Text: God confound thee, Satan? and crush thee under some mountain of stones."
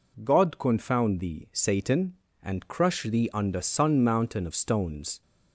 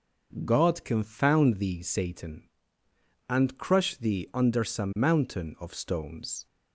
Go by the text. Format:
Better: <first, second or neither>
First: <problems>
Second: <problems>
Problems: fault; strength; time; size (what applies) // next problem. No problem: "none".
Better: second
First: says "sun" for "some"; at 3.6 s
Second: none